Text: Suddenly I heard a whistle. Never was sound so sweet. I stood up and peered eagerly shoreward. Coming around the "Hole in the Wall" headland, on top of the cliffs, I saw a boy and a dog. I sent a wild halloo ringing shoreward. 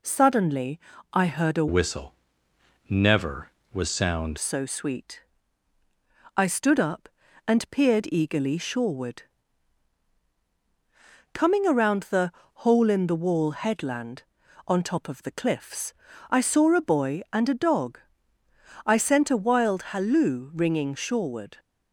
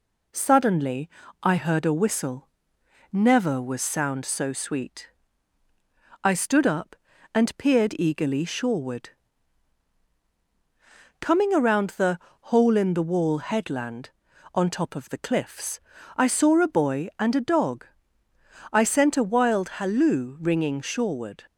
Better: second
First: pauses between "Suddenly" and "I"; slight; at 0.8 s; 0.32 s long // changes voice from "whistle" to "sound"; from 1.6 to 4.3 s; 2.7 s long // pauses between "the" and "Hole"; slight; at 12.3 s; 0.34 s long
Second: pauses between "Suddenly" and "I"; slight; at 1.0 s; 0.32 s long // pauses between "the" and "Hole"; slight; at 12.1 s; 0.34 s long

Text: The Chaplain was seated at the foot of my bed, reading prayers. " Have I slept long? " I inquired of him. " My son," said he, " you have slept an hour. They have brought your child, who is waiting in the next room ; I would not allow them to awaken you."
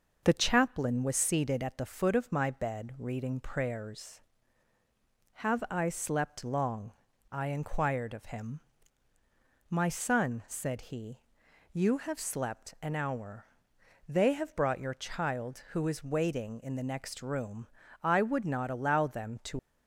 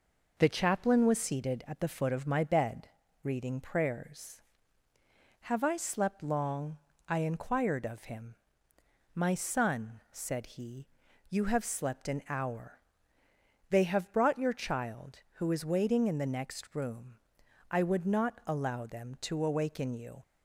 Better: second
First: starts louder than the rest; strong; until 1.2 s; 7.5 dB // stops before "awaken you"; at 19.5 s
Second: none

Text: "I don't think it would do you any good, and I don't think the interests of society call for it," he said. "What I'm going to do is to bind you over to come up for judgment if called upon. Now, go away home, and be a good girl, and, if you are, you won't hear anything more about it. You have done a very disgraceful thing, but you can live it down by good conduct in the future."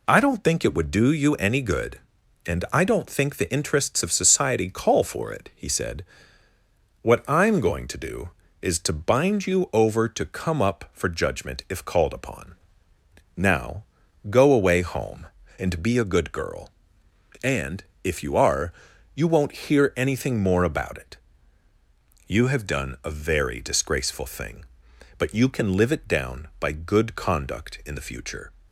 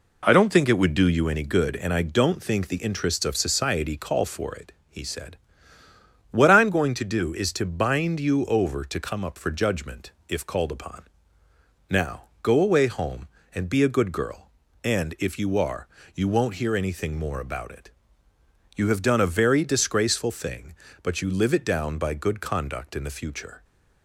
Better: first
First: none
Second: pauses between "judgment" and "if"; slight; at 10.1 s; 0.18 s long // skips "can"; at 21.2 s

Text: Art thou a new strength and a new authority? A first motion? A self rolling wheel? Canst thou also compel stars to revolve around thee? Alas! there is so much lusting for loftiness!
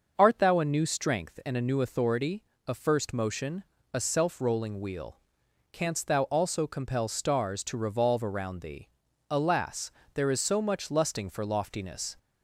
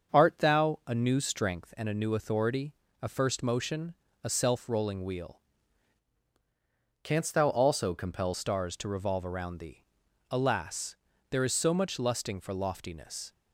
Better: first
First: starts louder than the rest; until 1.1 s; 6 dB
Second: starts louder than the rest; until 1.2 s; 6.5 dB // changes voice from "Canst" to "compel"; from 7.0 to 8.3 s; 1.3 s long

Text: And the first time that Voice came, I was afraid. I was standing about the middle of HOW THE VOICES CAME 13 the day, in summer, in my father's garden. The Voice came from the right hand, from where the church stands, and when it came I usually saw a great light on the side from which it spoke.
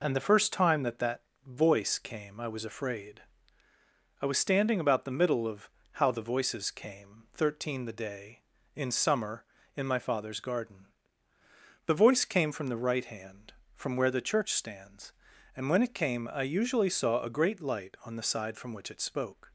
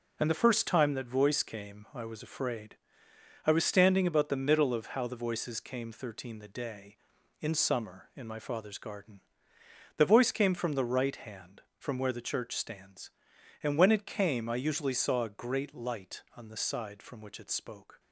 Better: second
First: says "that" twice; at 0.9 s // pauses between "of" and "HOW"; slight; at 5.6 s; 0.28 s long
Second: none

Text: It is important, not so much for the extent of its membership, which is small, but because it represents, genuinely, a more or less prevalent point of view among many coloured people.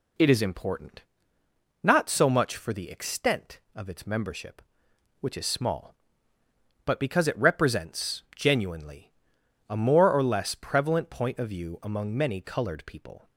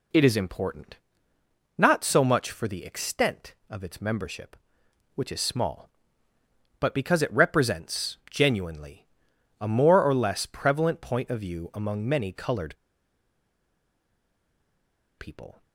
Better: first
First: none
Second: pauses between "coloured" and "people"; strong; at 12.7 s; 2.4 s long

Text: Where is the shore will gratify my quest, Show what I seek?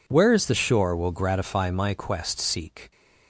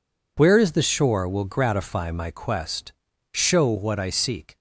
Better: second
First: skips "Show what I"; at 2.3 s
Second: none

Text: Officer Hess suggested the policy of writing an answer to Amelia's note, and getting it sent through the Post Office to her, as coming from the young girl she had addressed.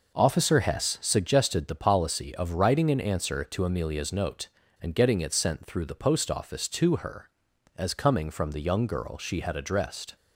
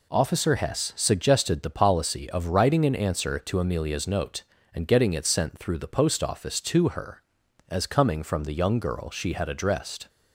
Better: second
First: starts louder than the rest; noticeable; until 1.1 s; 5.5 dB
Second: none

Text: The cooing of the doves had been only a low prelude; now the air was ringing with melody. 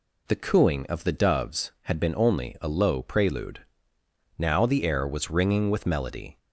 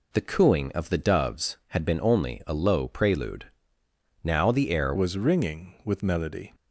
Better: first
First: none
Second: changes voice at "was"; from 4.9 s on; 1.6 s long

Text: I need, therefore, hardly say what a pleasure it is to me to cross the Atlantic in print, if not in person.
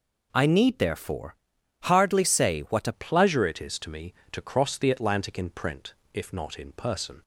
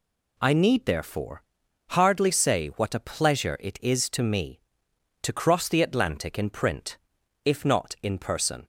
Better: second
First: changes voice at "pleasure"; from 2.9 s on; 4.3 s long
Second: none

